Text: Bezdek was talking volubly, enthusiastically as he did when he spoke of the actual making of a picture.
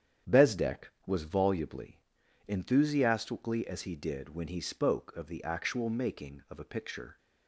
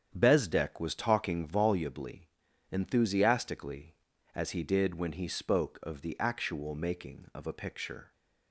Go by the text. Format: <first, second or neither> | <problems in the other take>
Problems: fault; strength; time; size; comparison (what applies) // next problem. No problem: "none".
second | starts louder than the rest; strong; until 1.4 s; 9 dB; strong in the second // skips "talking"; at 1.2 s